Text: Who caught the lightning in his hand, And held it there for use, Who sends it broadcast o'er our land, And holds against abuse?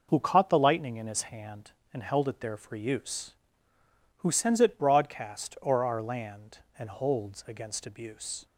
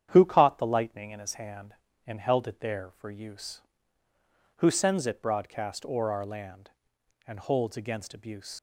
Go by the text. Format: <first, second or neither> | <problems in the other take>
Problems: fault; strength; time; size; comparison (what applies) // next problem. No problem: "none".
first | starts louder than the rest; strong; until 1.1 s; 9 dB // leaves "abuse" unfinished; at 8.5 s; 65 ms